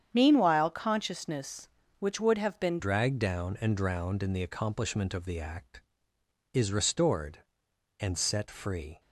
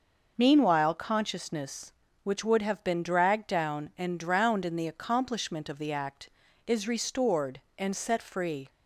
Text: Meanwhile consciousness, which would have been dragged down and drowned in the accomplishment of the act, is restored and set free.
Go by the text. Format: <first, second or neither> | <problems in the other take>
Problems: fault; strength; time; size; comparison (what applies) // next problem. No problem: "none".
second | starts louder than the rest; strong; until 1.1 s; 8.5 dB // changes voice at "dragged"; from 2.7 s on; 6.2 s long